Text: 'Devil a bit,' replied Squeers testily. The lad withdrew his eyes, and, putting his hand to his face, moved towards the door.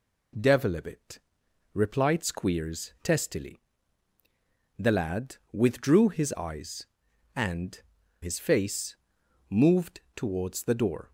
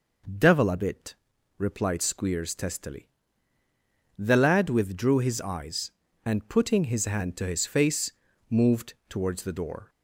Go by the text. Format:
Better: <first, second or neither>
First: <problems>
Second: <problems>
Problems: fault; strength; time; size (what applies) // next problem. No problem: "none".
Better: second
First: pauses between "lad" and "withdrew"; slight; at 5.3 s; 0.16 s long // skips "putting his hand to"; at 8.0 s // pauses between "moved" and "towards"; slight; at 9.9 s; 0.16 s long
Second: pauses between "moved" and "towards"; slight; at 8.9 s; 0.16 s long